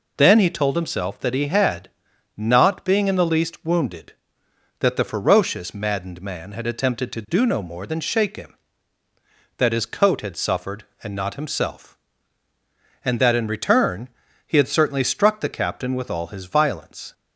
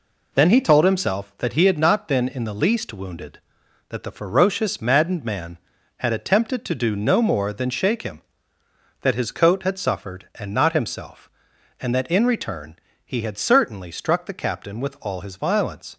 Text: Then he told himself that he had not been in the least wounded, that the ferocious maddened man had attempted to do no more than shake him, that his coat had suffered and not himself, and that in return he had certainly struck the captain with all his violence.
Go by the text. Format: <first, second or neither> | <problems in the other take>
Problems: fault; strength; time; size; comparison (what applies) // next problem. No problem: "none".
second | pauses between "had" and "not"; noticeable; at 1.8 s; 0.48 s long // says "being" for "been"; at 2.8 s // pauses between "return" and "he"; at 14.0 s; 0.40 s long; slight in the second